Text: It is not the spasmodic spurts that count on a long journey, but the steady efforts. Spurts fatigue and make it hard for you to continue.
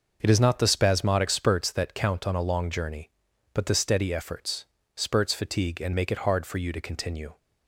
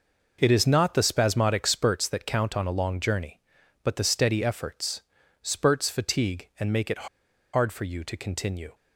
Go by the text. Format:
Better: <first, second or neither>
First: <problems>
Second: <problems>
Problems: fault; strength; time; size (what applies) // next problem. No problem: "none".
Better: first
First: none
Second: pauses between "it" and "hard"; noticeable; at 7.0 s; 0.46 s long